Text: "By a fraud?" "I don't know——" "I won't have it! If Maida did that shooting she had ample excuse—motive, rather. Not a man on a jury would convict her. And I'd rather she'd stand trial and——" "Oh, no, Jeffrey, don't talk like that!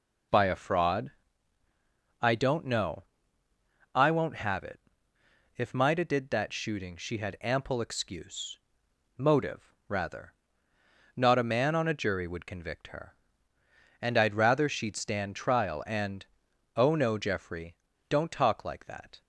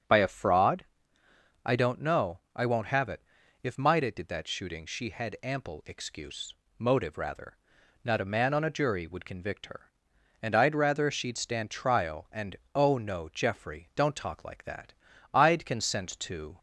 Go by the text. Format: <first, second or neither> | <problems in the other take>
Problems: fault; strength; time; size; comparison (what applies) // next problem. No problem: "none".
first | starts louder than the rest; strong; until 1.8 s; 7 dB // goes on to say "I'd consent to"; noticeable; from 15.3 s on; 1.2 s long